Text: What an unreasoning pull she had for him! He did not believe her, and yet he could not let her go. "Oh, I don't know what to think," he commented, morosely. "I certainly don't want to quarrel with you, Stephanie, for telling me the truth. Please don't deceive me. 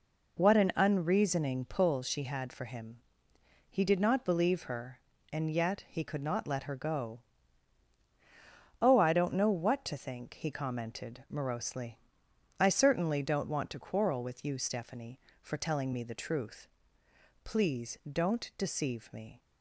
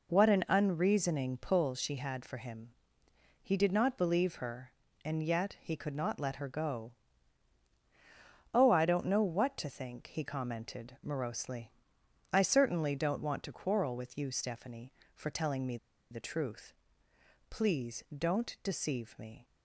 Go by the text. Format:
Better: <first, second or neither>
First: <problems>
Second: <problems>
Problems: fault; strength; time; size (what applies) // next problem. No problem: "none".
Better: first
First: pauses between "Please" and "don't"; slight; at 17.9 s; 0.16 s long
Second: pauses between "me" and "the"; slight; at 15.7 s; 0.34 s long // pauses between "Please" and "don't"; slight; at 18.0 s; 0.16 s long